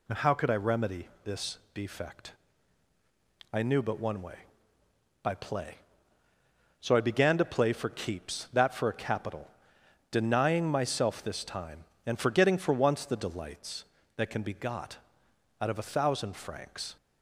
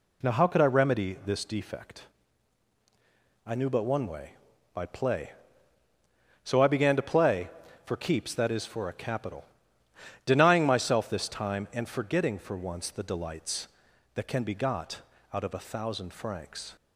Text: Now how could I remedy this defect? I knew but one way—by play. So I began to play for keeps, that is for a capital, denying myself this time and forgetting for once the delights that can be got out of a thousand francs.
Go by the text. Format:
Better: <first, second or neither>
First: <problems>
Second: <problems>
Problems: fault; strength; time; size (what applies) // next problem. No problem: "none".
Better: second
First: pauses between "remedy" and "this"; slight; at 1.0 s; 0.16 s long // pauses between "this" and "defect"; slight; at 1.5 s; 0.16 s long // skips "is"; at 8.7 s // pauses between "got" and "out"; noticeable; at 14.9 s; 0.62 s long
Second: pauses between "got" and "out"; slight; at 15.0 s; 0.32 s long